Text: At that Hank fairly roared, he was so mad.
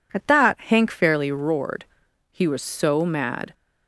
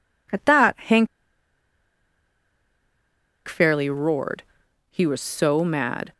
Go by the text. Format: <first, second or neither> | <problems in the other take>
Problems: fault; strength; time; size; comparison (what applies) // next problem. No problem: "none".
first | pauses between "Hank" and "fairly"; strong; at 1.0 s; 2.4 s long